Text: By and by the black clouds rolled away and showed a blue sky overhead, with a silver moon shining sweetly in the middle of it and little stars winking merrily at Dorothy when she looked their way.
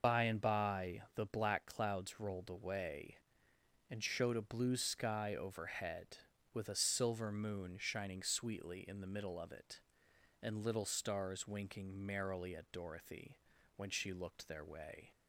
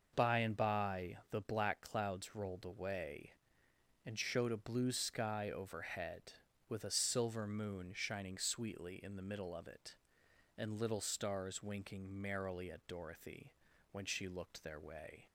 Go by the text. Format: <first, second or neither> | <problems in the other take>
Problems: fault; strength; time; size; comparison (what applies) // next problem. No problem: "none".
second | loses the start of "By"; at 0.0 s; 65 ms // pauses between "by" and "the"; slight; at 1.0 s; 0.16 s long; slight in the second // pauses between "Dorothy" and "when"; at 13.3 s; 0.40 s long; also in the second